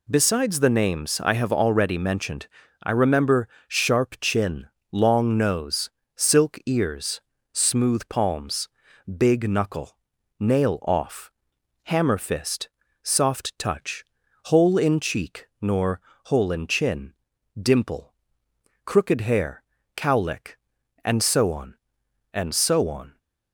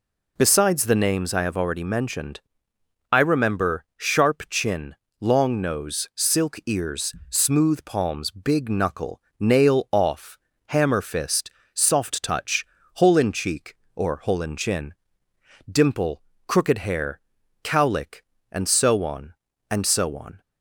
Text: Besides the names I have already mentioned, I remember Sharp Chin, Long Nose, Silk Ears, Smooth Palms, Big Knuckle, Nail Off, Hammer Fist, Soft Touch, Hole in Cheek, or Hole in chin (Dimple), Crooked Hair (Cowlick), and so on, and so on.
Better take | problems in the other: second | pauses between "remember" and "Sharp"; slight; at 3.4 s; 0.22 s long // says "nor" for "or"; at 15.5 s

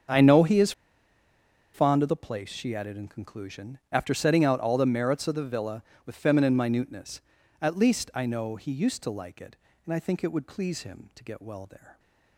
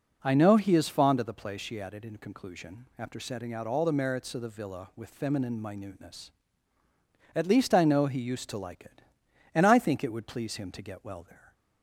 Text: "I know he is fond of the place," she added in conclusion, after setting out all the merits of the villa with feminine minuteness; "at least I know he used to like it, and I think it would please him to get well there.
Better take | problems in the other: second | starts louder than the rest; until 2.1 s; 7 dB // pauses between "is" and "fond"; at 0.7 s; 1.0 s long

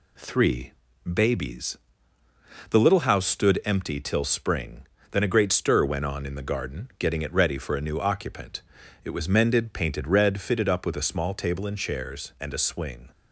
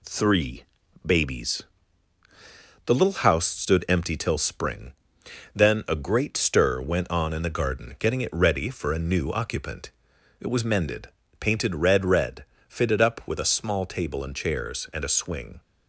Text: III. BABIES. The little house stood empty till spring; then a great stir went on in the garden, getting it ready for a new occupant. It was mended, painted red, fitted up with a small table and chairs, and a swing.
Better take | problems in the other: first | says "red" twice; at 12.0 s

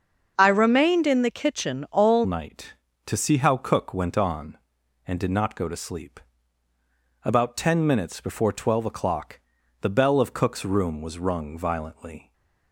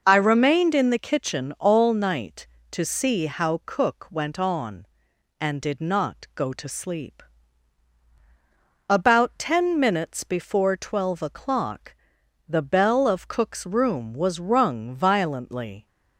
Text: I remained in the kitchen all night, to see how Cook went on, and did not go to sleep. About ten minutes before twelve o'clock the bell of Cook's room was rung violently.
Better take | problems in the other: second | starts louder than the rest; until 1.3 s; 7 dB // changes voice at "night"; from 2.2 s on; 10.1 s long // pauses between "o'clock" and "the"; at 9.3 s; 0.44 s long; noticeable in the second // stays silent after the last word; slight; from 12.2 s on; 0.5 s long

